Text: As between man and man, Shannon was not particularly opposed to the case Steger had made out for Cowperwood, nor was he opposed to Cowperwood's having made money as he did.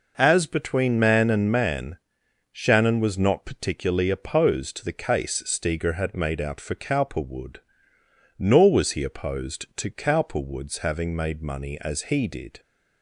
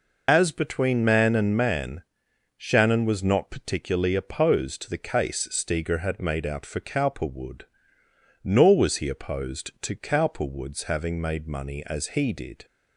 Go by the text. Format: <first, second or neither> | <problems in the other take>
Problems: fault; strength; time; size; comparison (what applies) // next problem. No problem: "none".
first | loses the start of "As"; at 0.2 s; 65 ms